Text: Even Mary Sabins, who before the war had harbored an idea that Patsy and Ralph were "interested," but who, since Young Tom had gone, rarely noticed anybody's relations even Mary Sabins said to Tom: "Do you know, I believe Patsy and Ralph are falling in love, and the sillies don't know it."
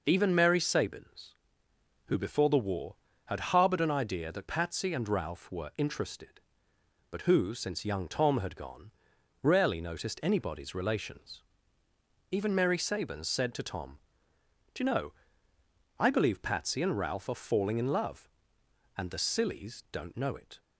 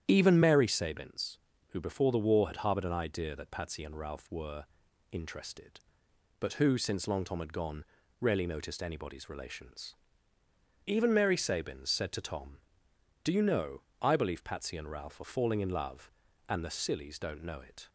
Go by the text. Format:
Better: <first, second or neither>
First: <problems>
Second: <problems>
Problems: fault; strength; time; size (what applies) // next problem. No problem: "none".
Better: first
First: pauses between "relations" and "even"; noticeable; at 11.4 s; 0.90 s long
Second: starts louder than the rest; strong; until 1.1 s; 10 dB // pauses between "were" and "interested"; at 4.6 s; 0.44 s long // says "Long" for "Young"; at 7.0 s // pauses between "relations" and "even"; noticeable; at 9.9 s; 0.90 s long